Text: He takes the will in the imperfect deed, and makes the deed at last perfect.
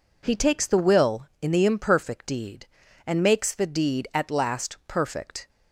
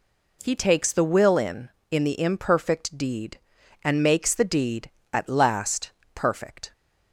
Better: first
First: none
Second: says "in" twice; at 1.8 s // pauses between "last" and "perfect"; slight; at 5.8 s; 0.24 s long

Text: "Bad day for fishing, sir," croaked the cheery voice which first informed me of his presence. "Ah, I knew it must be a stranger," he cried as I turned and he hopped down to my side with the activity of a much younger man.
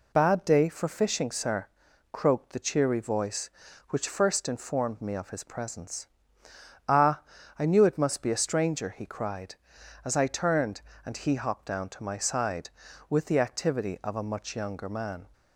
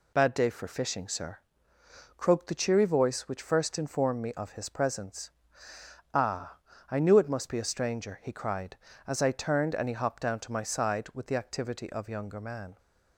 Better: first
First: none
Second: skips "a much"; at 12.0 s

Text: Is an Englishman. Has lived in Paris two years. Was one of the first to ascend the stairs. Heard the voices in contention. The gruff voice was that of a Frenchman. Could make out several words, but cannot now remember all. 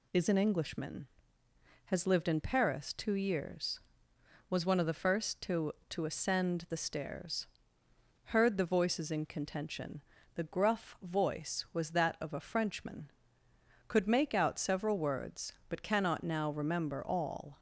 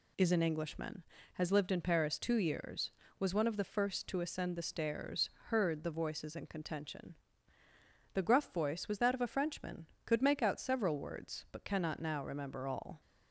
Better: second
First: says "to" twice; at 5.9 s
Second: none

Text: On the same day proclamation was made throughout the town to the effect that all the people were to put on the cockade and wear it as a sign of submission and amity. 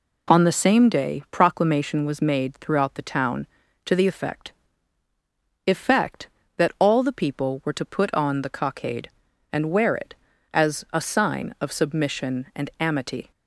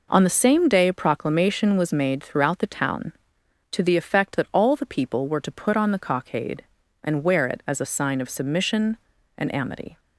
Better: second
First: says "effect" twice; at 5.6 s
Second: none

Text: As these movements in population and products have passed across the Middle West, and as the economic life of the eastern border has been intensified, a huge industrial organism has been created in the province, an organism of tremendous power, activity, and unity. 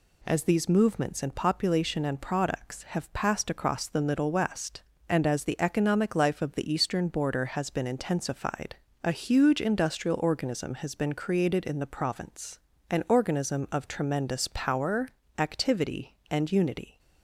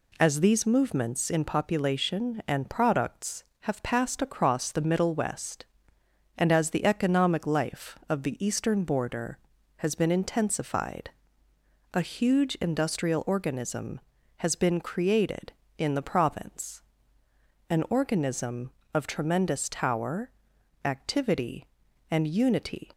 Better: first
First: none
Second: says "tower" for "power"; at 19.6 s

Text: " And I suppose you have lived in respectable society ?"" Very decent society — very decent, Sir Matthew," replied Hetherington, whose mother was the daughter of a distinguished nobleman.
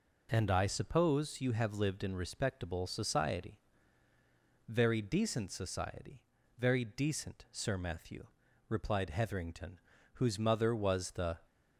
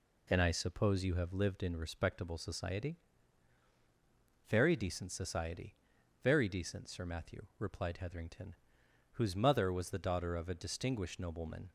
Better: second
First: stops before "daughter of a distinguished nobleman"; at 11.4 s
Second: none

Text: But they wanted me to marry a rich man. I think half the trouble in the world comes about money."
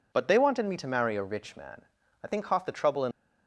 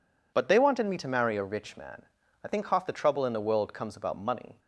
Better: second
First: stops before "the world comes about money"; at 3.1 s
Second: none

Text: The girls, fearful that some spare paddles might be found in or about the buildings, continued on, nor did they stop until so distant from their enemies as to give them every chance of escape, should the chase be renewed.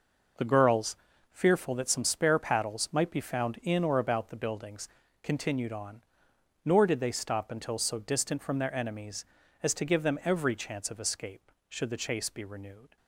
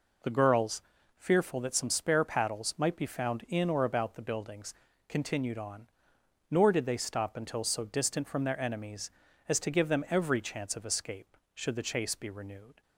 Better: second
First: gets quieter; strong; throughout; 10.5 dB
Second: none

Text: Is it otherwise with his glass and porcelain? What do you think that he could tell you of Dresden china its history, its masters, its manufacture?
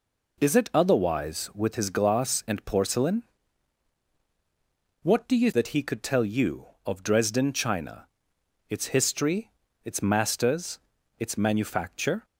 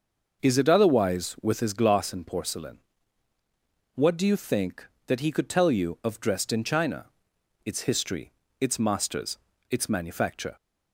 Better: second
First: skips "think"; at 5.5 s // pauses between "china" and "its"; noticeable; at 8.0 s; 0.64 s long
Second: pauses between "china" and "its"; noticeable; at 7.0 s; 0.58 s long

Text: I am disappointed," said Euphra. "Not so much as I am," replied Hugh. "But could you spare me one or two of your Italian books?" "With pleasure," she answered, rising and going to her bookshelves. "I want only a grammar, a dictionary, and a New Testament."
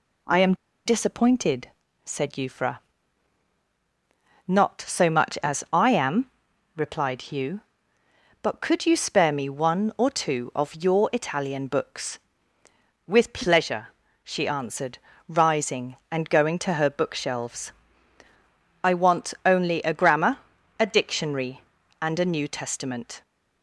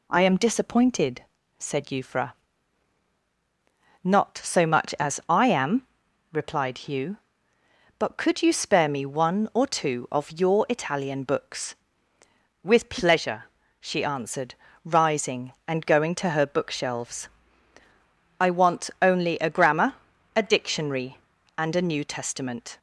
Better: second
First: pauses between "am" and "disappointed"; slight; at 0.5 s; 0.30 s long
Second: none

